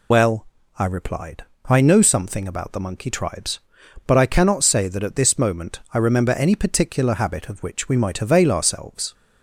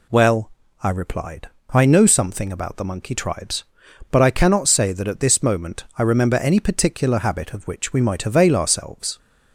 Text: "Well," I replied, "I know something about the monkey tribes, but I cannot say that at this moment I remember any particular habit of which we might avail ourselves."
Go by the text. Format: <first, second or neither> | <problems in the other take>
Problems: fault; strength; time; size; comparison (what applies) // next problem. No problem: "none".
second | loses the start of "Well"; at 0.1 s; 50 ms